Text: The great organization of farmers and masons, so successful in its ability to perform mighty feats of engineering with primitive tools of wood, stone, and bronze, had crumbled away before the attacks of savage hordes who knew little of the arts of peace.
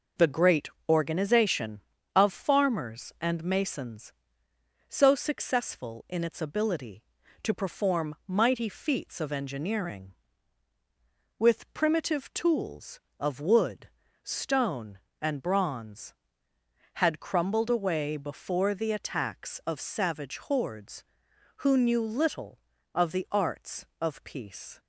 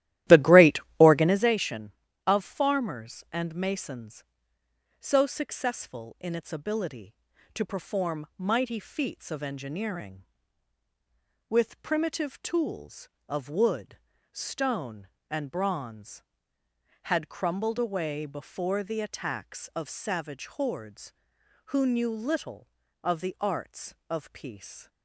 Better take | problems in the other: first | starts louder than the rest; strong; until 1.5 s; 14.5 dB // pauses between "great" and "organization"; slight; at 0.8 s; 0.18 s long; slight in the first

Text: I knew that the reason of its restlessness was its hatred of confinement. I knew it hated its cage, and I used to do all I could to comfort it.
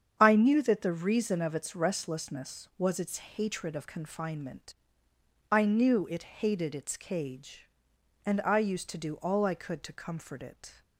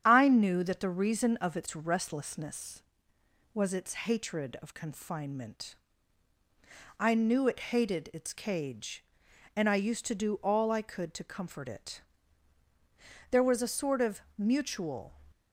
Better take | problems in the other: first | starts louder than the rest; strong; until 1.0 s; 8.5 dB; strong in the first // goes on to say "There was a sort of mutual"; strong; from 13.3 s on; 1.8 s long

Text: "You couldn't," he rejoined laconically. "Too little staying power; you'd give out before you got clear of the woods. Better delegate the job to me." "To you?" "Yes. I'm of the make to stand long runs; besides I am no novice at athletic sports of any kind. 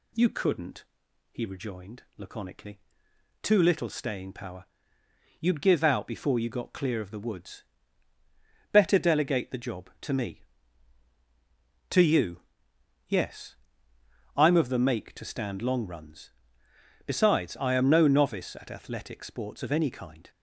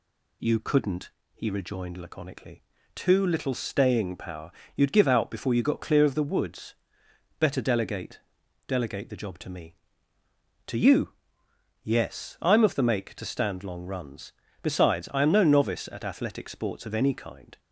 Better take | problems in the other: first | says "delegate" twice; at 8.6 s

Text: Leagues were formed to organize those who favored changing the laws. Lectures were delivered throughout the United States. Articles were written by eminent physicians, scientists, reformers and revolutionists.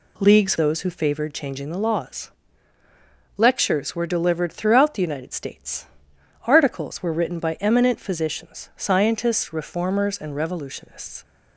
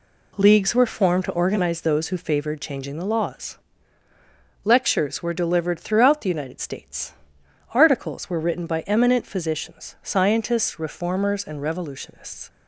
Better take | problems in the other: second | skips "were formed to organize"; at 0.5 s

